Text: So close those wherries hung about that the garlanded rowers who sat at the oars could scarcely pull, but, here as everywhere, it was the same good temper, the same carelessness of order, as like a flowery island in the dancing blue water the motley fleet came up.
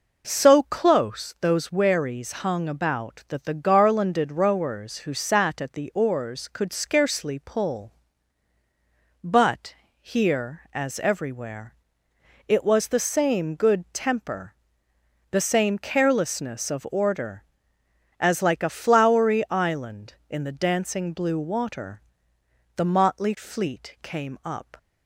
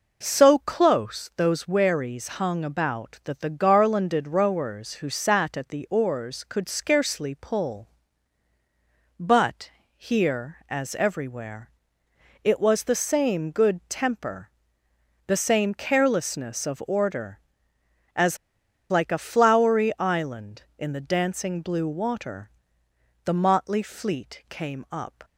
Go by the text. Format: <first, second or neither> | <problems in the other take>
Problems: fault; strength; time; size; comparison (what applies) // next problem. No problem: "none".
first | pauses between "as" and "like"; noticeable; at 18.3 s; 0.53 s long // pauses between "water" and "the"; noticeable; at 22.5 s; 0.74 s long; noticeable in the first